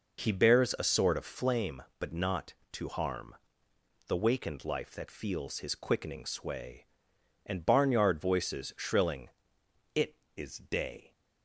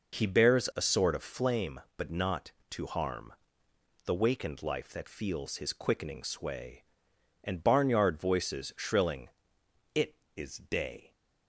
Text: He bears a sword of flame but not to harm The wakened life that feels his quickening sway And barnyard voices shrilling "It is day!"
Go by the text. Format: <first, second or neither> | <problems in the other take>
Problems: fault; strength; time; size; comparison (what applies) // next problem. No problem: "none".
neither | pauses between "harm" and "The"; noticeable; the same in both // pauses between "shrilling" and "It"; noticeable; the same in both